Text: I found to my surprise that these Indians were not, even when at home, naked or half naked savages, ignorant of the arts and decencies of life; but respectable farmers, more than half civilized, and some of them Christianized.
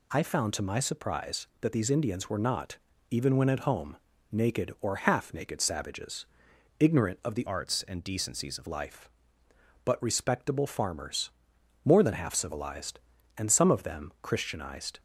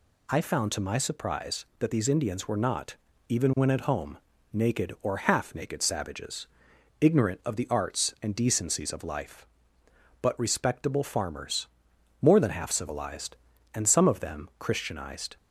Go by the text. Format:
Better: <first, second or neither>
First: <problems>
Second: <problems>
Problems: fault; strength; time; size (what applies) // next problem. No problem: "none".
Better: second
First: changes voice from "arts" to "of"; from 7.4 to 8.6 s; 1.2 s long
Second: none